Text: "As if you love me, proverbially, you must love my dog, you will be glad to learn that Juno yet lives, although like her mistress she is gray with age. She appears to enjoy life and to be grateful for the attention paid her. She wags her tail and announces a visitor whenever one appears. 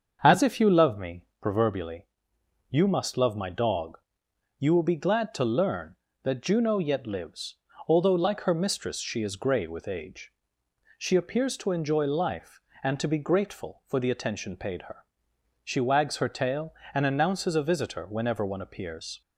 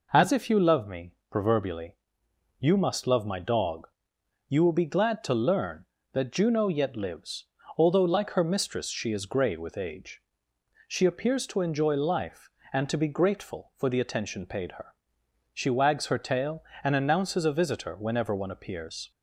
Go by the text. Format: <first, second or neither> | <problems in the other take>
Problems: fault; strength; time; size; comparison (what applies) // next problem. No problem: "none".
second | starts louder than the rest; until 1.5 s; 7 dB